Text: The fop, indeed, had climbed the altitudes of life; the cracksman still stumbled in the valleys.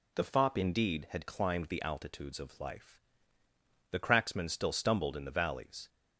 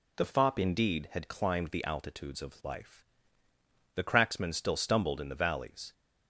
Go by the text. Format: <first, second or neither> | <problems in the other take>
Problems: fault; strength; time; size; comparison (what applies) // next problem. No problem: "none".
neither | none